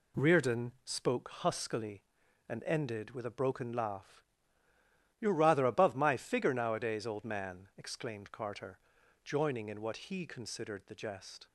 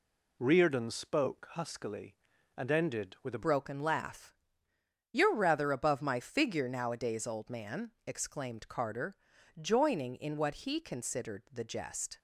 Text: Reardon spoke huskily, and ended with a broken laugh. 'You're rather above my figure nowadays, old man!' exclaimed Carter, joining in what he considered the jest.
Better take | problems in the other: first | changes voice at "broken"; from 3.4 s on; 8.7 s long

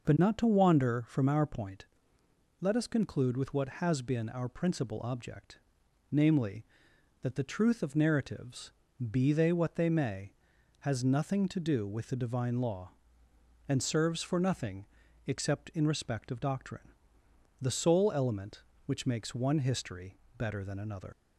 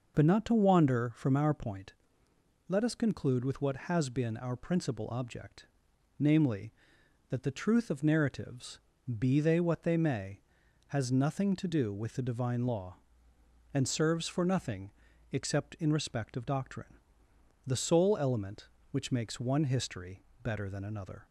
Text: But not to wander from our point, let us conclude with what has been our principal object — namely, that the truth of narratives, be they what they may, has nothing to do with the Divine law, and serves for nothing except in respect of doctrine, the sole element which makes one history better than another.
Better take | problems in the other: second | pauses between "nothing" and "except"; at 14.8 s; 0.40 s long; also in the second // pauses between "history" and "better"; slight; at 20.1 s; 0.22 s long; slight in the second // leaves "another" unfinished; at 21.1 s; 70 ms

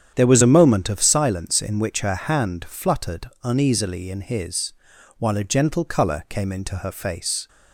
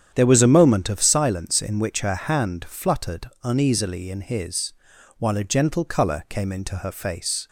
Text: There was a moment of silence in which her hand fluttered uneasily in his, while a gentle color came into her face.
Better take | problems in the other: neither | starts louder than the rest; strong; the same in both

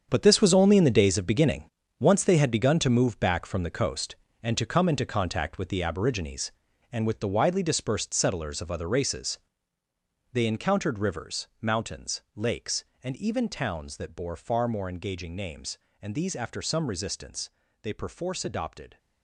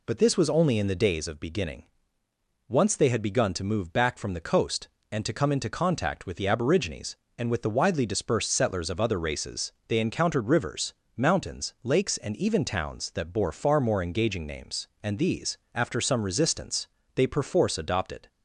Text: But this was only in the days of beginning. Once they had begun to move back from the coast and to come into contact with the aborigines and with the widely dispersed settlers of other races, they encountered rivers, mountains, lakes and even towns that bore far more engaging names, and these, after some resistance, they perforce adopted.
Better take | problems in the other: second | gets quieter; strong; throughout; 11.5 dB

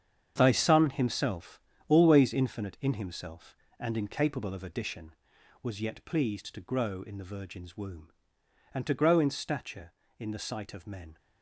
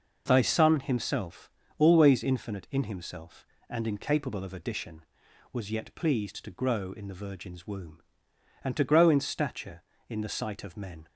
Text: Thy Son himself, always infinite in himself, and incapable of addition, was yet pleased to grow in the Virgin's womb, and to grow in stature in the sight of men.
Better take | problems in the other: second | gets quieter; strong; throughout; 11 dB

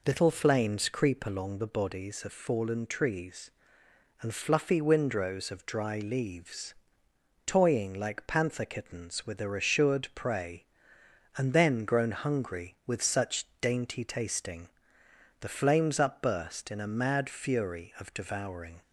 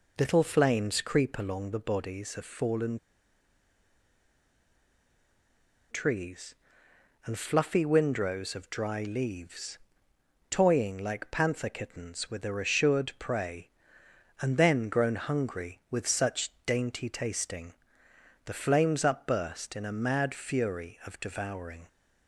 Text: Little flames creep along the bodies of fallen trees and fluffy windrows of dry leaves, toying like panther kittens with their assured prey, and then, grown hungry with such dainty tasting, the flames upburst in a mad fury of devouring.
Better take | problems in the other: first | pauses between "fallen" and "trees"; strong; at 2.9 s; 2.9 s long

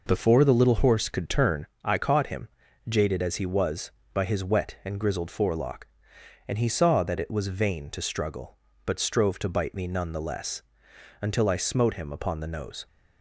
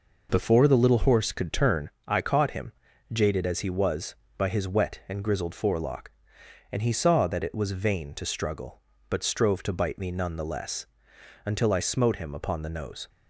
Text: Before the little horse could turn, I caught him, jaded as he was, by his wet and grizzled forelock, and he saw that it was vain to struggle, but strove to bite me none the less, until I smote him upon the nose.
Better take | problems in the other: neither | none

